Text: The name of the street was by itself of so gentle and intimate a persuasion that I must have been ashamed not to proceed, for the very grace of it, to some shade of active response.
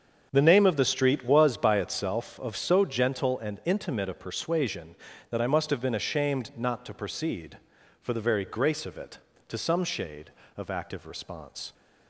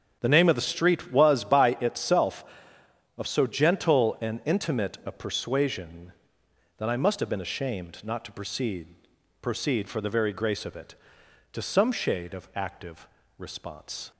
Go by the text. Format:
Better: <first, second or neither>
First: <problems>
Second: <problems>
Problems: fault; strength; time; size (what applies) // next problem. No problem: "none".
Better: first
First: starts louder than the rest; until 1.3 s; 7 dB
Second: starts louder than the rest; strong; until 1.2 s; 7.5 dB // says "proceed" twice; at 9.4 s // pauses between "active" and "response"; slight; at 13.0 s; 0.30 s long